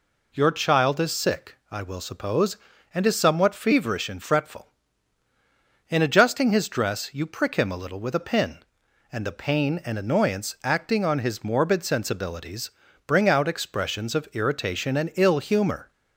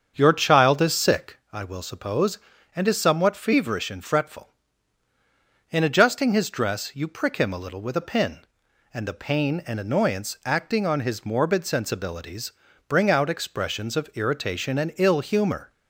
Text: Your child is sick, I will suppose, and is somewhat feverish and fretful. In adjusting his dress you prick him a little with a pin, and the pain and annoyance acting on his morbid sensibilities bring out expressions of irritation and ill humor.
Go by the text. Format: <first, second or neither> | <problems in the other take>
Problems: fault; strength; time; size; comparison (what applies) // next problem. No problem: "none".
first | starts louder than the rest; strong; until 1.4 s; 7 dB // pauses between "sensibilities" and "bring"; slight; at 12.5 s; 0.36 s long; slight in the first